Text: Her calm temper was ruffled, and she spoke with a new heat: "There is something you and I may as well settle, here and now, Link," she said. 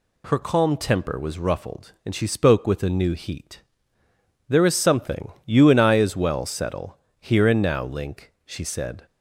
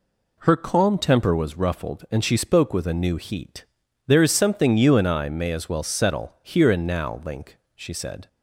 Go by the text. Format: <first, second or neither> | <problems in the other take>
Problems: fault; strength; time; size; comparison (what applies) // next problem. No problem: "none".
second | skips "may"; at 5.9 s